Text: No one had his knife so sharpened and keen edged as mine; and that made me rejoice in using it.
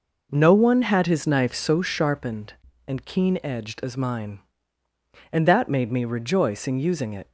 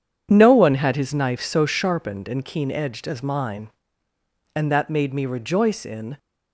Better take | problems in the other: first | starts louder than the rest; strong; until 1.3 s; 8 dB // stops before "using it"; at 6.1 s

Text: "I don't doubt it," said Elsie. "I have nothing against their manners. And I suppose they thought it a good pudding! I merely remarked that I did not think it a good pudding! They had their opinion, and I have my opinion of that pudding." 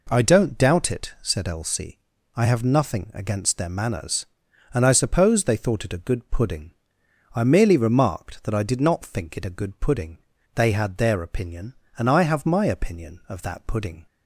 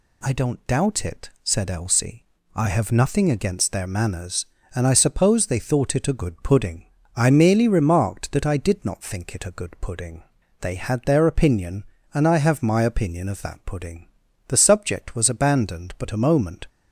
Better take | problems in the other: first | goes on to say "The subject was abandoned but a moment"; strong; from 14.4 s on; 2.2 s long

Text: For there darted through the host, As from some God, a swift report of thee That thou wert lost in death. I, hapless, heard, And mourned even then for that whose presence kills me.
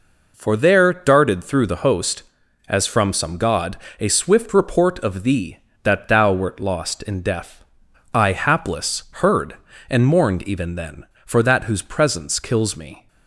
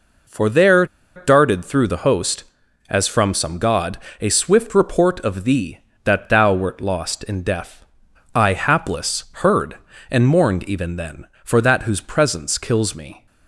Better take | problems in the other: first | pauses between "there" and "darted"; slight; at 0.8 s; 0.29 s long

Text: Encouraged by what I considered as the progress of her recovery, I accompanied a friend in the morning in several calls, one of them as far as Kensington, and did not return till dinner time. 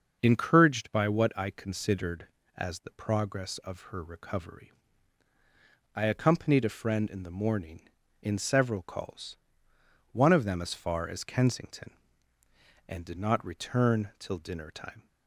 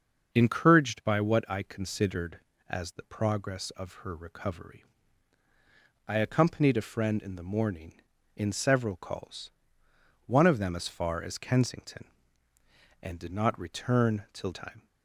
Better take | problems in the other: first | starts louder than the rest; until 1.3 s; 6.5 dB; also in the first // skips "dinner"; at 14.5 s

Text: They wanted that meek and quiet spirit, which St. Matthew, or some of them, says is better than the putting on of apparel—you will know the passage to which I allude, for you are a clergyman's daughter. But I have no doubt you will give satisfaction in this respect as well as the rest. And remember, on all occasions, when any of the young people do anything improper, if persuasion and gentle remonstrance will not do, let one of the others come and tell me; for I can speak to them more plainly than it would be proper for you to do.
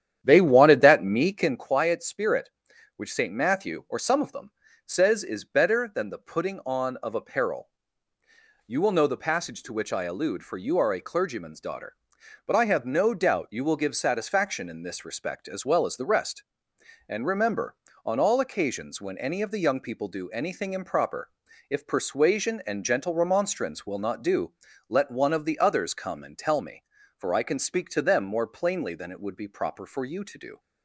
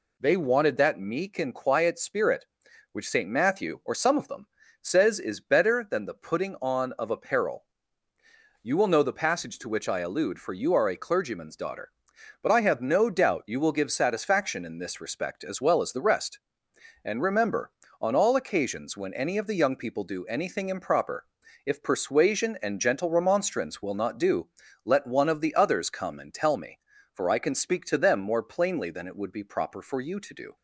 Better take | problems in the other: second | starts louder than the rest; strong; until 1.7 s; 10 dB

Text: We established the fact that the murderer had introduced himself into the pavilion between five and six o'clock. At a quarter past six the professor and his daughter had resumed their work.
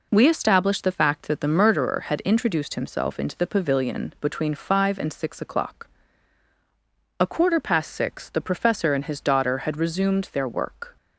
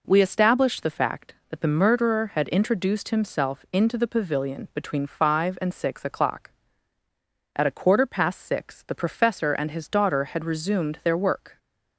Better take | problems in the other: second | skips "At"; at 6.5 s

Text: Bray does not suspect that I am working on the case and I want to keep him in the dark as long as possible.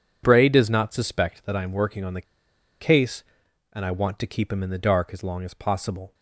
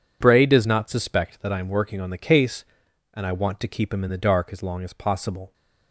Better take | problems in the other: second | pauses between "the" and "case"; noticeable; at 2.2 s; 0.60 s long

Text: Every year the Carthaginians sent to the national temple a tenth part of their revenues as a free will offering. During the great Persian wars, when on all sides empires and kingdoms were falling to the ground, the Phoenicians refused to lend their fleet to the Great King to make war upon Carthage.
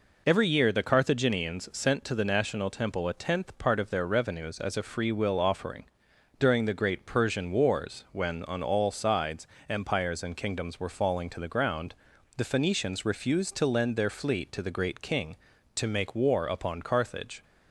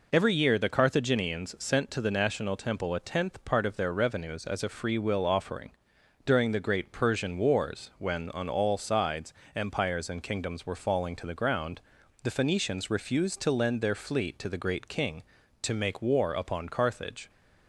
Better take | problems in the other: neither | pauses between "sides" and "empires"; slight; the same in both

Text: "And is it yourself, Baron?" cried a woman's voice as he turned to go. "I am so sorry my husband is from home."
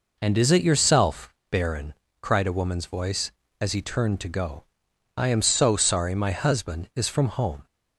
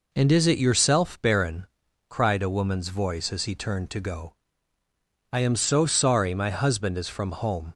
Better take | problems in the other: neither | none

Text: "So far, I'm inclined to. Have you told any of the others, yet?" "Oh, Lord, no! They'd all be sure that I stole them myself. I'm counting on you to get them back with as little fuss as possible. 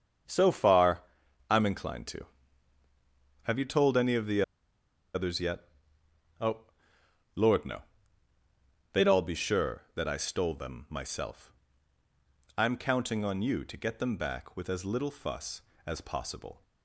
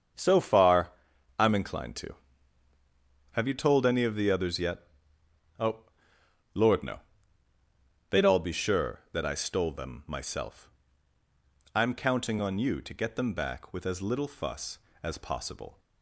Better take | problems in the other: second | starts louder than the rest; strong; until 1.7 s; 7 dB; strong in the second // pauses between "the" and "others"; noticeable; at 4.4 s; 0.71 s long

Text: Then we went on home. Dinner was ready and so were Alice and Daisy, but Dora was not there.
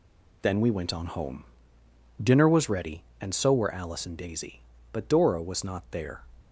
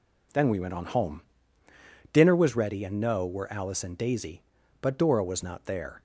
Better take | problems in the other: first | says "no" for "so"; at 2.9 s

